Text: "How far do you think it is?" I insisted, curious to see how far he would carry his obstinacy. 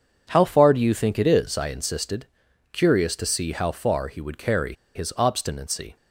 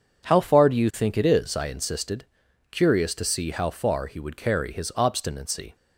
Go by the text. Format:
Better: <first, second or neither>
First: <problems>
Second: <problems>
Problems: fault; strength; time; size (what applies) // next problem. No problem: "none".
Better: second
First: pauses between "carry" and "his"; slight; at 4.7 s; 0.20 s long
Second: none